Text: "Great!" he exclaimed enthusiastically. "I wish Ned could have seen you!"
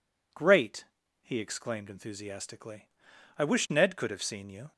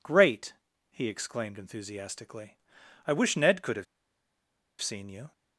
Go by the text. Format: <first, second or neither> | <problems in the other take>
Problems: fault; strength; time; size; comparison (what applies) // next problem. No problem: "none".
first | pauses between "have" and "seen"; noticeable; at 3.8 s; 0.96 s long